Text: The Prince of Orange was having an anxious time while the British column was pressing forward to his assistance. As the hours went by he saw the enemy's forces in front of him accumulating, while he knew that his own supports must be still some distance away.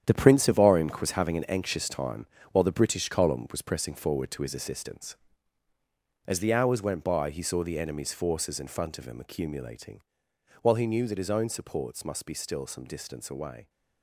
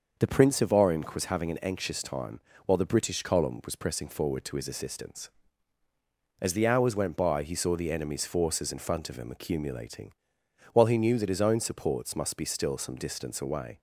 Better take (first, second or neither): second